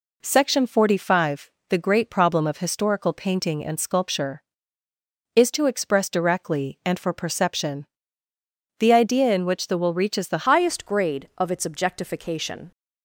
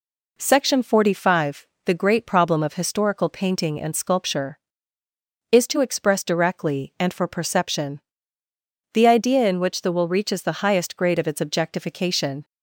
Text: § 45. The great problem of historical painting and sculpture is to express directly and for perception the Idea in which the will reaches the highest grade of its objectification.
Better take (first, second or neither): second